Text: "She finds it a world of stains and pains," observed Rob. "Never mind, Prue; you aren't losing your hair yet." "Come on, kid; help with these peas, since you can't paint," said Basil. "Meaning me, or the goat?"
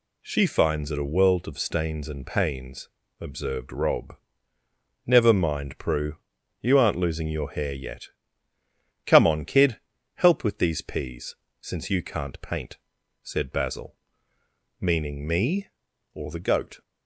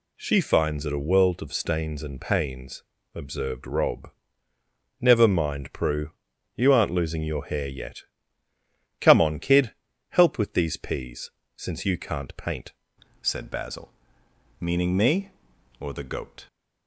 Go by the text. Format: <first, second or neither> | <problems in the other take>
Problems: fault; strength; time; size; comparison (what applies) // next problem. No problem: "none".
first | changes voice at "said"; from 13.2 s on; 3.2 s long